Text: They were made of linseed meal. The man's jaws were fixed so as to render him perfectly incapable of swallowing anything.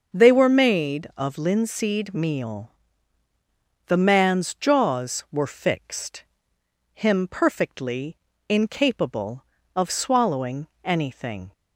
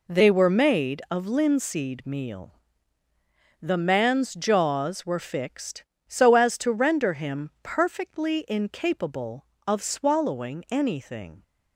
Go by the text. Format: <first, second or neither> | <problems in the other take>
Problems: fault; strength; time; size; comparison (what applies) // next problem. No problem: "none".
second | starts louder than the rest; noticeable; until 1.2 s; 6 dB // skips "so as to render"; at 6.5 s // pauses between "perfectly" and "incapable"; slight; at 8.1 s; 0.32 s long // pauses between "swallowing" and "anything"; slight; at 10.6 s; 0.18 s long